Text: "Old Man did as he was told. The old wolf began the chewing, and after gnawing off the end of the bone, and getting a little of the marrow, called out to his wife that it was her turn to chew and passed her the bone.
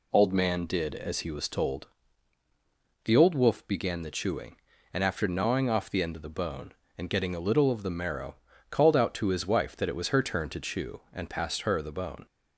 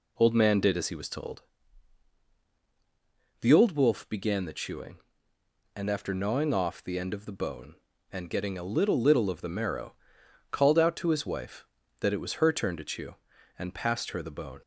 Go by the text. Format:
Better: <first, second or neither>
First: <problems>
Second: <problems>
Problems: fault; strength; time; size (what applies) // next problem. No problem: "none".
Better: first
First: none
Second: says "little" twice; at 9.0 s